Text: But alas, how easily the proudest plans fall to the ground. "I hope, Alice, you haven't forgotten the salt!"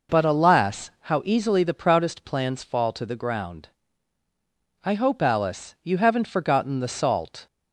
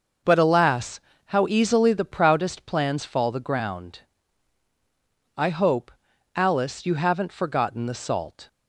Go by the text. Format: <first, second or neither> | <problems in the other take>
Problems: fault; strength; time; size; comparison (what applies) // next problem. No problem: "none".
first | skips "to"; at 3.2 s